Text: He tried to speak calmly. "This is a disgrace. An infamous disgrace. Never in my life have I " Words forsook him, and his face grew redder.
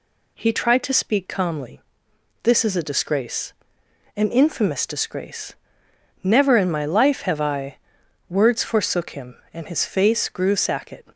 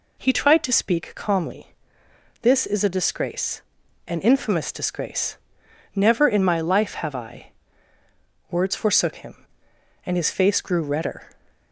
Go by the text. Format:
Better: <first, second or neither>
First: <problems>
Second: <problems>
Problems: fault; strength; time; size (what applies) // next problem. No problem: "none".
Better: second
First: says "sacket" for "redder"; at 10.5 s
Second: none